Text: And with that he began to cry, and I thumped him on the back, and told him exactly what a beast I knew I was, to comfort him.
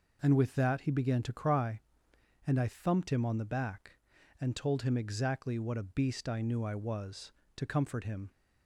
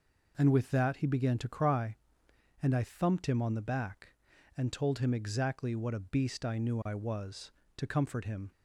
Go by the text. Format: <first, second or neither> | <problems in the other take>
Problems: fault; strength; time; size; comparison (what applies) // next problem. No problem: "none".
neither | none